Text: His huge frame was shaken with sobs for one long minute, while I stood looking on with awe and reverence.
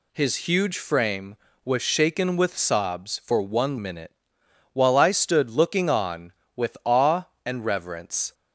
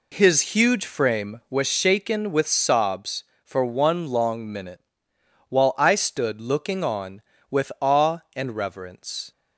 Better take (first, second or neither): second